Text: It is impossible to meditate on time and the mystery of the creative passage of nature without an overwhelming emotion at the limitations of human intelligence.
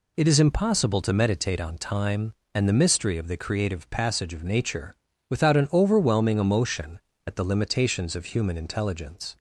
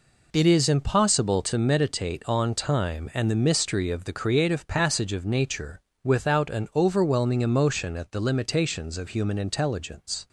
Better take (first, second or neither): neither